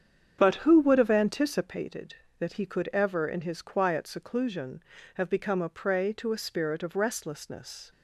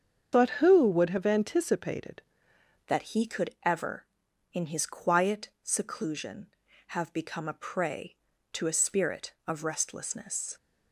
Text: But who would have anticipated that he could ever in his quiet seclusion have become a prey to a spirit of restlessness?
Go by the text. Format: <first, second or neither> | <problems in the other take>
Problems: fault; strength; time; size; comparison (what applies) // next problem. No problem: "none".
first | starts louder than the rest; strong; until 1.3 s; 7 dB; strong in the first // changes voice at "that"; from 2.8 s on; 7.7 s long